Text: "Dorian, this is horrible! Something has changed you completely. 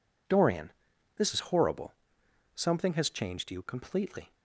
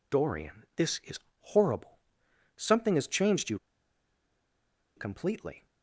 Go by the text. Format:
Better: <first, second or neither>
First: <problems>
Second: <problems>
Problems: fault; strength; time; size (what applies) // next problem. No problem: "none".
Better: first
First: none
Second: pauses between "is" and "horrible"; slight; at 1.1 s; 0.22 s long // pauses between "you" and "completely"; strong; at 3.5 s; 1.3 s long